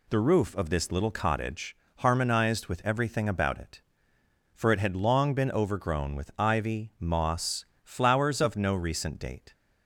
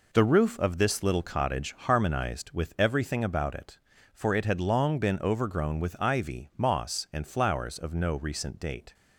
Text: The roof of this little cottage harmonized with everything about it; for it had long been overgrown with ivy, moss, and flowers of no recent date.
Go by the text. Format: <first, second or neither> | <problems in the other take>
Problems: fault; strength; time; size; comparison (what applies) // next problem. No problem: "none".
second | pauses between "cottage" and "harmonized"; slight; at 1.7 s; 0.20 s long // skips "and"; at 7.7 s